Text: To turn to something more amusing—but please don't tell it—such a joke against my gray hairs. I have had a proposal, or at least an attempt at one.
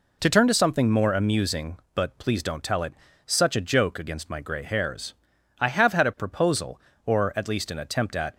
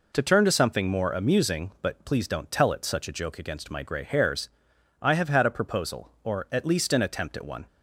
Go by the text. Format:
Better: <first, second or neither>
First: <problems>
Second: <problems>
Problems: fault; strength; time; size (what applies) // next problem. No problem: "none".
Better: second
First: stops before "one"; at 8.3 s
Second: none